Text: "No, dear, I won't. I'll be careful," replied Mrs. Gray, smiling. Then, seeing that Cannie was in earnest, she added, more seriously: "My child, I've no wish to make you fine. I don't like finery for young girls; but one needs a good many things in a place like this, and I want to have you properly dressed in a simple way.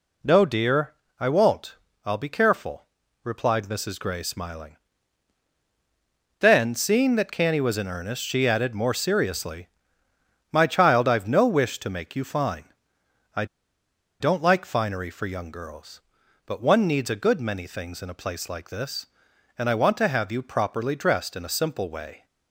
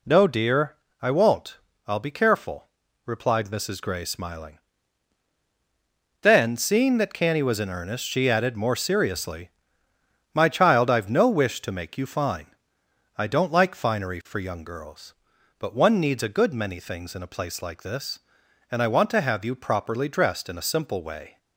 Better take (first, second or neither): second